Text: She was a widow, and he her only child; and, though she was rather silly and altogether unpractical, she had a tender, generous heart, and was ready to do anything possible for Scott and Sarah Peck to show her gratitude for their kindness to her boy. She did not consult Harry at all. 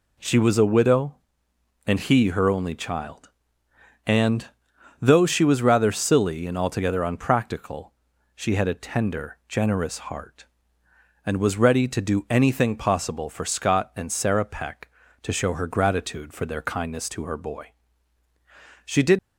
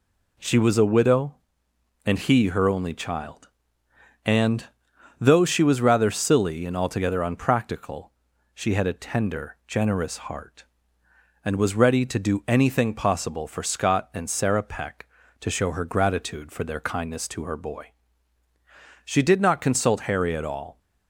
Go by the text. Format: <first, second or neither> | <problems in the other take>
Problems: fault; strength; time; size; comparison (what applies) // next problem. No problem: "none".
second | stops before "not consult Harry at all"; at 19.1 s